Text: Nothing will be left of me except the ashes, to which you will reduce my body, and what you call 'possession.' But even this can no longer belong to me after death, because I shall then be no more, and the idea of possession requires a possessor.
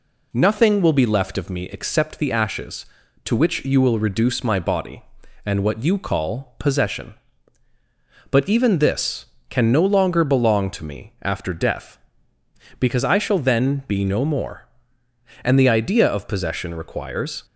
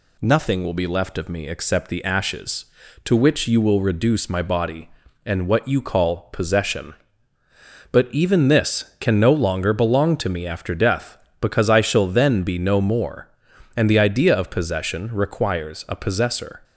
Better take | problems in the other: second | stops before "a possessor"; at 17.4 s

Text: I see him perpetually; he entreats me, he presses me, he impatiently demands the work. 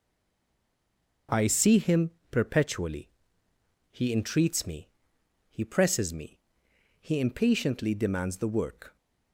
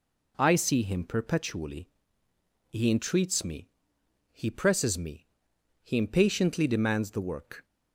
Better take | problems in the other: second | stays silent before the first word; noticeable; until 1.2 s; 1.2 s long // pauses between "him" and "perpetually"; slight; at 2.0 s; 0.22 s long

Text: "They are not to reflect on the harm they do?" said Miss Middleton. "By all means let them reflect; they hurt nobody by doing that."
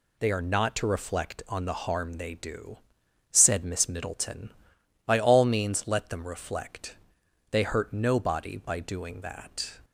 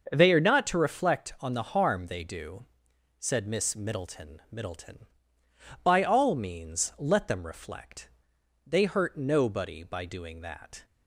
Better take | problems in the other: first | starts louder than the rest; until 1.1 s; 6.5 dB // says "Middleton" twice; at 4.5 s

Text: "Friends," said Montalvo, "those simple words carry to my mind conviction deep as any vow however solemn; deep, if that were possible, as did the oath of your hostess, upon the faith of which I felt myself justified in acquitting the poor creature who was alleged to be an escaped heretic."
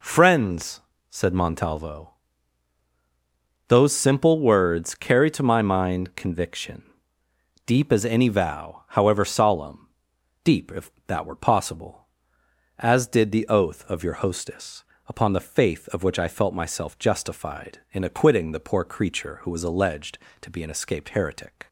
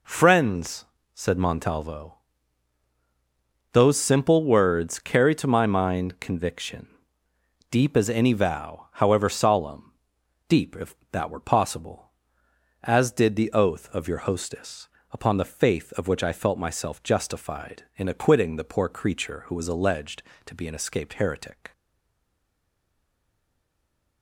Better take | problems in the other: first | pauses between "conviction" and "deep"; noticeable; at 6.8 s; 0.86 s long; noticeable in the first // stays silent after the last word; from 21.7 s on; 2.5 s long

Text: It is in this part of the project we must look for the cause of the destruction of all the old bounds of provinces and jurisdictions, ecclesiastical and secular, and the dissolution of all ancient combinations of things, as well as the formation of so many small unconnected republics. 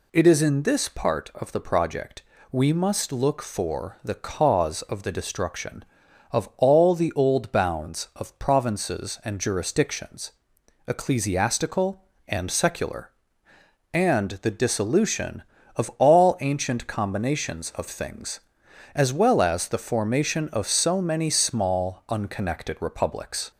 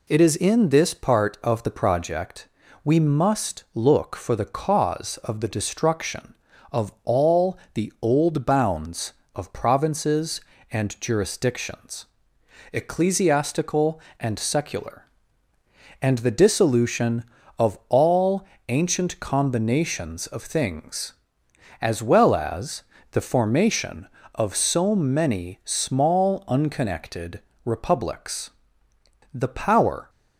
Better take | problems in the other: first | pauses between "project" and "we"; slight; at 2.4 s; 0.34 s long; slight in the first // pauses between "all" and "the"; slight; at 7.5 s; 0.15 s long // pauses between "all" and "ancient"; slight; at 18.4 s; 0.24 s long // pauses between "as" and "the"; slight; at 22.8 s; 0.28 s long // pauses between "unconnected" and "republics"; slight; at 27.4 s; 0.24 s long // goes on to say "The power"; noticeable; from 29.3 s on; 0.76 s long

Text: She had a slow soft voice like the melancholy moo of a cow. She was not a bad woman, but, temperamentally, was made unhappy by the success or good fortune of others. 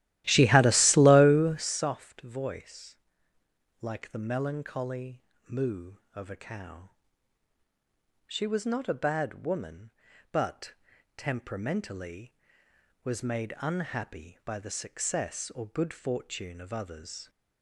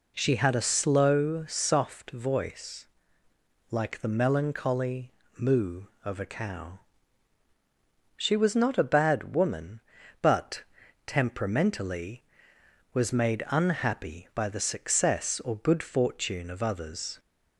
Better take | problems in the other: second | starts louder than the rest; strong; until 1.8 s; 15 dB // pauses between "voice" and "like"; noticeable; at 2.9 s; 0.82 s long; noticeable in the second // pauses between "melancholy" and "moo"; slight; at 5.2 s; 0.26 s long; slight in the second

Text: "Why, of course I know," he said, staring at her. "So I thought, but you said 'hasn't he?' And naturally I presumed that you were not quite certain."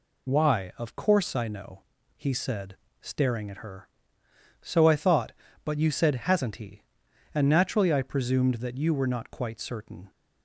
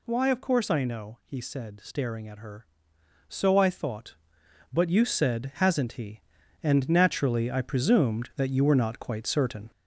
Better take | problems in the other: first | gets louder; noticeable; throughout; 4 dB

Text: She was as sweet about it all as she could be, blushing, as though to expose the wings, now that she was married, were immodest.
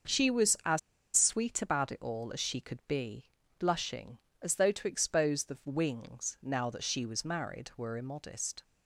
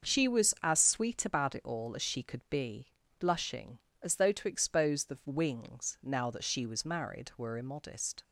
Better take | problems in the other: second | starts louder than the rest; noticeable; until 1.5 s; 6 dB; also in the second // pauses between "as" and "sweet"; at 0.7 s; 0.36 s long

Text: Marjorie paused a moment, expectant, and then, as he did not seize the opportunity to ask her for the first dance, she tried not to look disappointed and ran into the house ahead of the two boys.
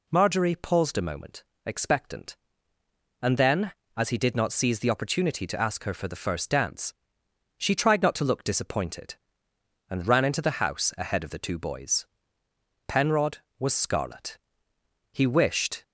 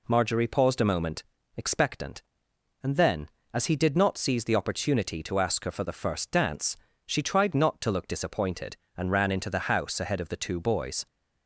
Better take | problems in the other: second | goes on to say "Penrod was scarlet he wished"; strong; from 12.8 s on; 2.9 s long

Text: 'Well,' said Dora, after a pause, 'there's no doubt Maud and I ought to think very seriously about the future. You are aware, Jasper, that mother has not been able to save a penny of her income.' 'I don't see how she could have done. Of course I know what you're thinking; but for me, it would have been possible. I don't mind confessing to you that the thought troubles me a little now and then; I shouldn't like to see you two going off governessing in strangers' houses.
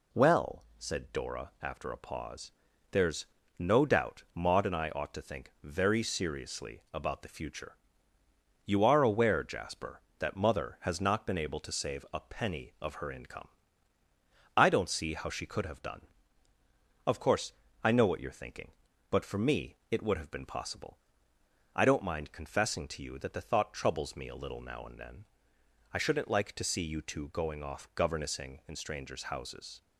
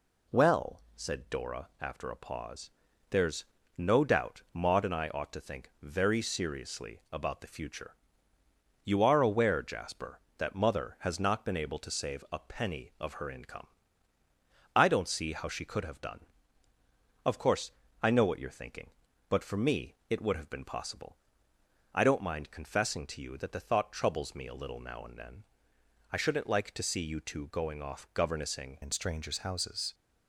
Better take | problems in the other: first | pauses between "there's" and "no"; slight; at 3.4 s; 0.32 s long; slight in the first // pauses between "course" and "I"; slight; at 17.7 s; 0.30 s long; slight in the first // changes voice at "in"; from 28.8 s on; 1.1 s long

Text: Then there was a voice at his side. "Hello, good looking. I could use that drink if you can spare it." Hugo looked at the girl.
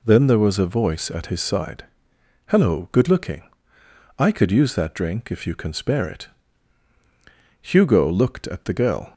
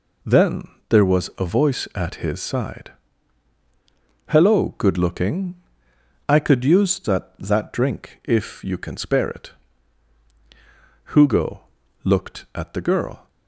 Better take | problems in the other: first | pauses between "Then" and "there"; slight; at 0.6 s; 0.22 s long // says "that" twice; at 7.3 s // pauses between "Hugo" and "looked"; at 11.6 s; 0.42 s long

